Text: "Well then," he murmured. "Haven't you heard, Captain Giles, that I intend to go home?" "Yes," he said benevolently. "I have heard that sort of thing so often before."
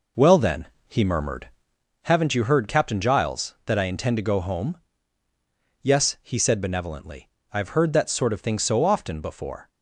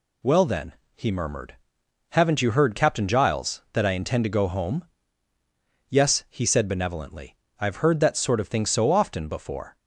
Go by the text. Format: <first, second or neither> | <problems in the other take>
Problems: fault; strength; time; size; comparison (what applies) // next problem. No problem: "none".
second | starts louder than the rest; noticeable; until 1.9 s; 4 dB